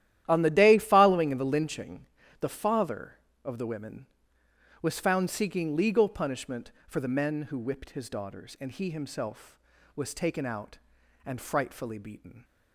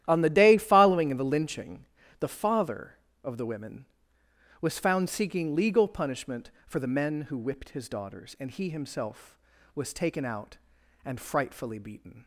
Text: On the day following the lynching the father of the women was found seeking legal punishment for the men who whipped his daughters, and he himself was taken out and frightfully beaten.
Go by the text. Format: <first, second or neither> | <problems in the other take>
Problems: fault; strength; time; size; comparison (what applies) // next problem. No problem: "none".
neither | starts louder than the rest; strong; the same in both // pauses between "lynching" and "the"; slight; the same in both